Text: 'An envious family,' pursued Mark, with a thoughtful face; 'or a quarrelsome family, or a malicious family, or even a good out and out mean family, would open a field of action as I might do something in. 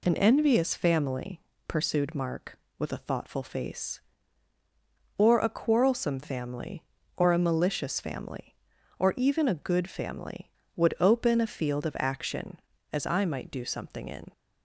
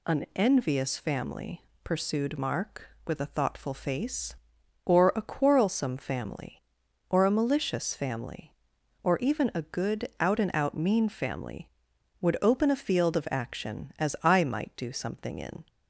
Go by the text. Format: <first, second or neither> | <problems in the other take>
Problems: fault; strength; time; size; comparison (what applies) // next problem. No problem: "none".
second | skips "out and out mean"; at 9.8 s